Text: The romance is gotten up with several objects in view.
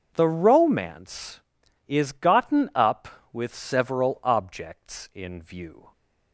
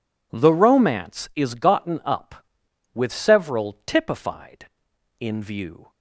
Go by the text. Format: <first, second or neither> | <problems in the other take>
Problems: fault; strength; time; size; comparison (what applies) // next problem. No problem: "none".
first | says "typified" for "objects"; at 3.8 s